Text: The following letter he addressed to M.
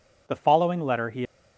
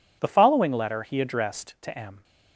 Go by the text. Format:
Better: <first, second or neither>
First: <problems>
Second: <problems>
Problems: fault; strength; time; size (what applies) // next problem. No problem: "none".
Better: second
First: stops before "addressed to M"; at 1.2 s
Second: none